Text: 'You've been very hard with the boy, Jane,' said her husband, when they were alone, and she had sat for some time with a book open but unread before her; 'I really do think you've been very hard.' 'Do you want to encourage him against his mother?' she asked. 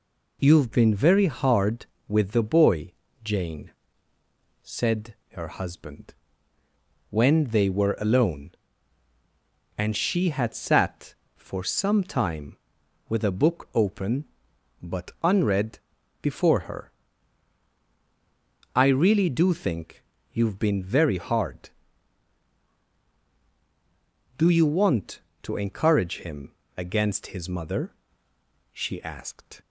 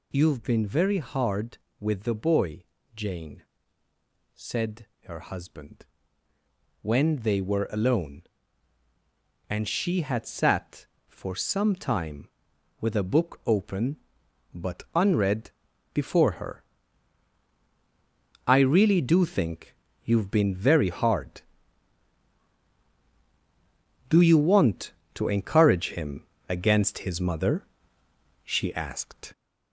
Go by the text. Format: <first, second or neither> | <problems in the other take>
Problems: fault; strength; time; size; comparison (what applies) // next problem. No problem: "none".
first | gets louder; noticeable; throughout; 4.5 dB // pauses between "said" and "her"; slight; at 4.8 s; 0.18 s long; slight in the first // pauses between "unread" and "before"; at 15.4 s; 0.44 s long; also in the first // pauses between "think" and "you've"; slight; at 19.7 s; 0.30 s long; slight in the first // pauses between "him" and "against"; slight; at 26.2 s; 0.24 s long; slight in the first